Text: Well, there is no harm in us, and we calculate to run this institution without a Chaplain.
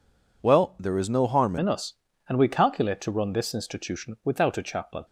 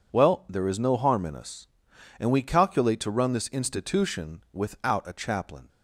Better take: second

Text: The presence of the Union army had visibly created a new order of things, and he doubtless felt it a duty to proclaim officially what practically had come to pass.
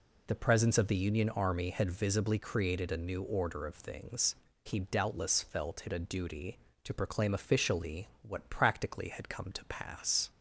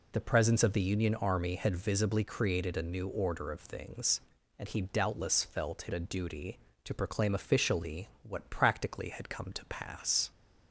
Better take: second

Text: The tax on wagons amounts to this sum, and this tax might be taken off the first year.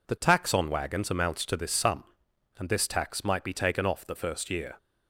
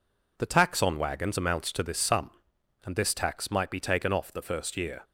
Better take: neither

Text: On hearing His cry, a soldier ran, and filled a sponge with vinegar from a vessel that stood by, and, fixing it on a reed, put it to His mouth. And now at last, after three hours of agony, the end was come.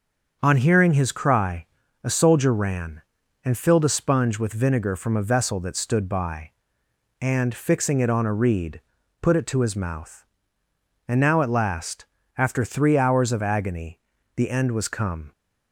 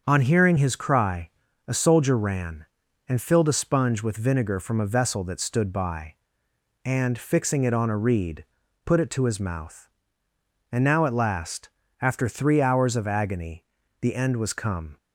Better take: neither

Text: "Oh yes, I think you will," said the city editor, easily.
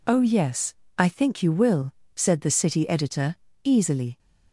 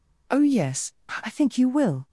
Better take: first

